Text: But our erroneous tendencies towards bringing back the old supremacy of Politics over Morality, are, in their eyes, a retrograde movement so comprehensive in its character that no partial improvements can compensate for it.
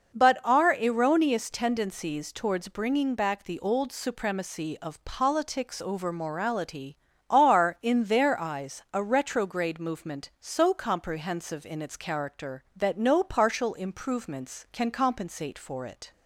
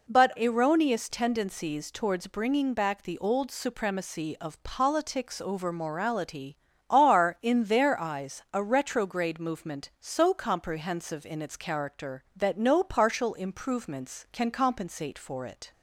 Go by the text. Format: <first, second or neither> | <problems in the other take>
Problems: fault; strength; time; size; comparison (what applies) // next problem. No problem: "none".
first | skips "our"; at 0.3 s